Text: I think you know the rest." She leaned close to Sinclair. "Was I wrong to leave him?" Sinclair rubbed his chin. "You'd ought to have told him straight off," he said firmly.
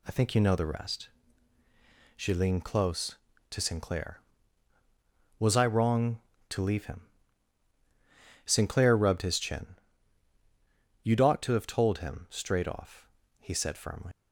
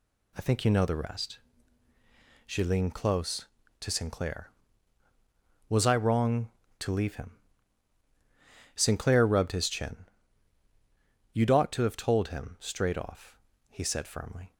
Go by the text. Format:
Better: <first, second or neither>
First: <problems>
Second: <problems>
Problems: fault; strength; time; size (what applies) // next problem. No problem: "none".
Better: second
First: leaves "firmly" unfinished; at 14.1 s; 115 ms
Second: none